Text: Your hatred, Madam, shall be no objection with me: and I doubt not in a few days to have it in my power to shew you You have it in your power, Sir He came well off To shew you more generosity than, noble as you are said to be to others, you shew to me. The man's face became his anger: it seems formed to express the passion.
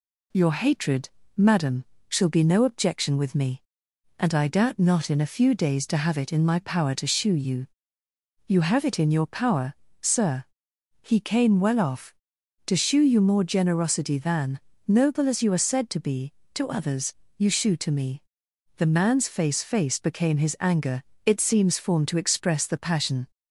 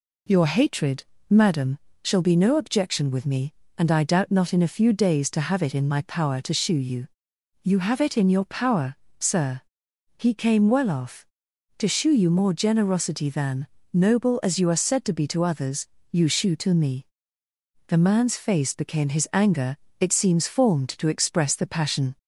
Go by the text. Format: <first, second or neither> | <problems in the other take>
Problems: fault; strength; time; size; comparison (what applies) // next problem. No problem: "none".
second | pauses between "you" and "You"; noticeable; at 7.6 s; 0.80 s long; noticeable in the second // pauses between "Sir" and "He"; noticeable; at 10.4 s; 0.58 s long; noticeable in the second // says "face" twice; at 19.6 s